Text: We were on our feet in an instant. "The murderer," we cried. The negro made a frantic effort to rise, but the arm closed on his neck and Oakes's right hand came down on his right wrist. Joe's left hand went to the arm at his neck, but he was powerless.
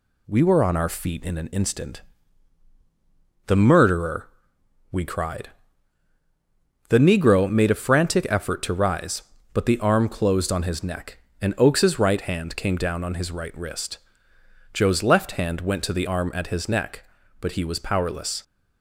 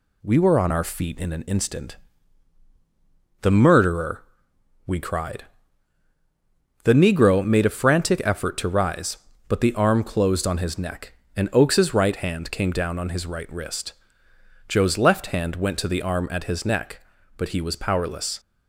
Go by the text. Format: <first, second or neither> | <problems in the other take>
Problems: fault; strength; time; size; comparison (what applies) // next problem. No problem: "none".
neither | none